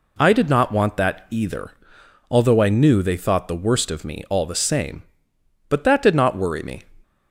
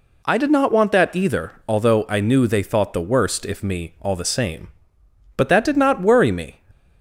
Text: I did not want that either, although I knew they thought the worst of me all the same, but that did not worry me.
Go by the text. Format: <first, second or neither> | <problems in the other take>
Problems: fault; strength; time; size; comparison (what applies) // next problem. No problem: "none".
first | says "if" for "of"; at 3.4 s